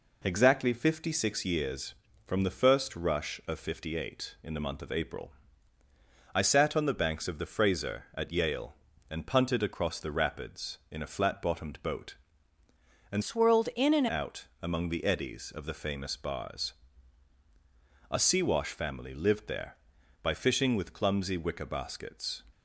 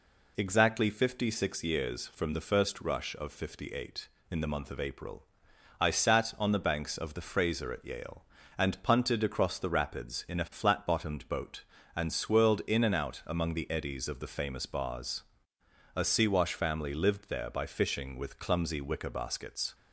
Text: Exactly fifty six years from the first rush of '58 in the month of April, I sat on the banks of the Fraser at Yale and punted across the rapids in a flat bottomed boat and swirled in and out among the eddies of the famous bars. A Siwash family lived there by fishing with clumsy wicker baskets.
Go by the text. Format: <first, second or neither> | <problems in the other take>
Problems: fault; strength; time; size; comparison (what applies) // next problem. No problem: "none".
second | changes voice from "swirled" to "and"; from 13.2 to 14.0 s; 0.8 s long